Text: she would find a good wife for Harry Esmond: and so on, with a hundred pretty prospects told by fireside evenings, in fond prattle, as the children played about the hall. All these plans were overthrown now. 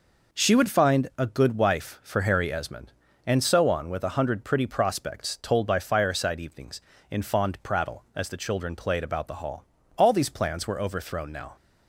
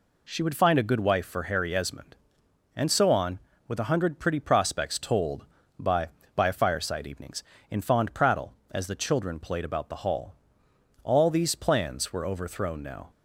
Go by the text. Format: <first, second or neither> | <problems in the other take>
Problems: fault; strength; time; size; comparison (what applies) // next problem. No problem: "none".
first | says "by" twice; at 6.3 s